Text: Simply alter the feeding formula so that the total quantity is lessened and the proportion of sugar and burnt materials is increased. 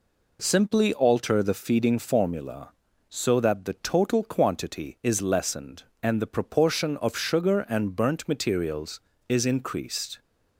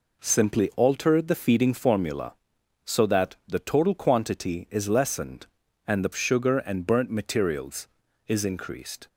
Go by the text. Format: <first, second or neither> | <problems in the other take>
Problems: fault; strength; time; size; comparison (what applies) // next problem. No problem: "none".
first | skips "proportion of"; at 6.1 s